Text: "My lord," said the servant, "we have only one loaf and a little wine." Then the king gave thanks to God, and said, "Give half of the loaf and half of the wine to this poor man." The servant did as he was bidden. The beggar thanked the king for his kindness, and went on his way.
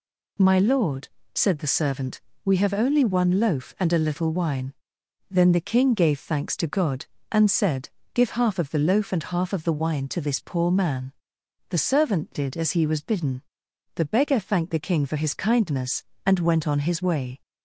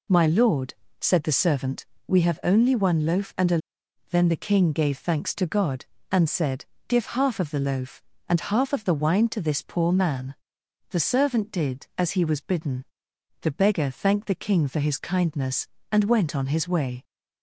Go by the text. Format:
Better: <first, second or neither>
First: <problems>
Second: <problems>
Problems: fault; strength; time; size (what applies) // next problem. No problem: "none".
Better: first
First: none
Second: skips "little wine"; at 3.8 s